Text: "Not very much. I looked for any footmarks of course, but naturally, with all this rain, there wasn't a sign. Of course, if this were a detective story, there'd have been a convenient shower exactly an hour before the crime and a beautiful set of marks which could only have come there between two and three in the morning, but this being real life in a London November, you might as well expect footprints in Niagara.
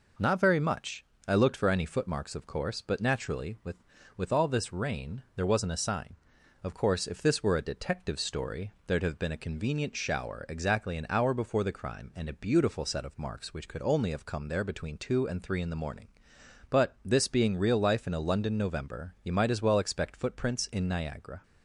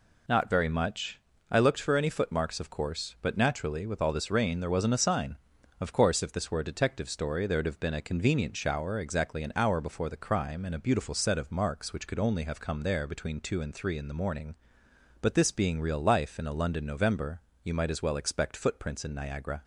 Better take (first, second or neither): second